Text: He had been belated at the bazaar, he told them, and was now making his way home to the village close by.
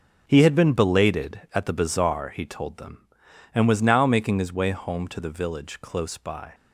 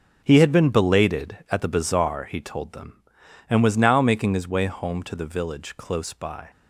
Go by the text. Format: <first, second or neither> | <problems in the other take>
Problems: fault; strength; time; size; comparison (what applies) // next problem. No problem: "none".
neither | none